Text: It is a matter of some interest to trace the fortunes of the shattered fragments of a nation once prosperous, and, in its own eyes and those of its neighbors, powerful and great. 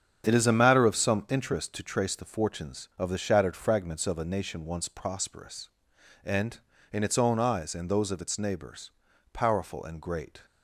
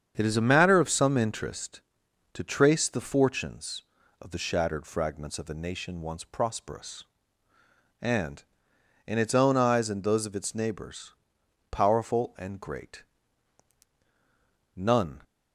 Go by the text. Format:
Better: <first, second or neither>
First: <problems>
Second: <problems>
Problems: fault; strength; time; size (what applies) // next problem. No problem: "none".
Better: first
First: starts louder than the rest; strong; until 1.3 s; 7.5 dB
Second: starts louder than the rest; strong; until 1.1 s; 7.5 dB // goes on to say "None"; slight; from 14.7 s on; 0.46 s long